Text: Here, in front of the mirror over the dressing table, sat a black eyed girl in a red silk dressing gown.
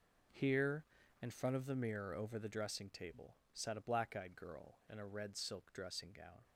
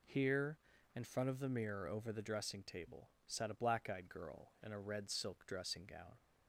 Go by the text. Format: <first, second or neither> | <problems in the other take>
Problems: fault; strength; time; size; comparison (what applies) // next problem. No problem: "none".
second | gets quieter; strong; throughout; 12 dB